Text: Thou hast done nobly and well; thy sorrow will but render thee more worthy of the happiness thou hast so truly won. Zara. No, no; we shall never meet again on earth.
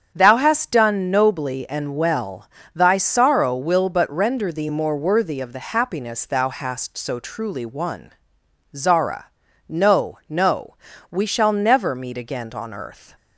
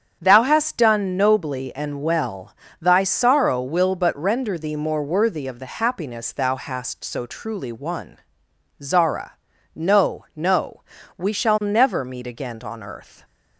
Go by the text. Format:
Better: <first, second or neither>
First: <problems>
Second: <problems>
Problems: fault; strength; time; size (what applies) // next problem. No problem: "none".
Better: neither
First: starts louder than the rest; strong; until 1.1 s; 7.5 dB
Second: starts louder than the rest; strong; until 1.2 s; 7.5 dB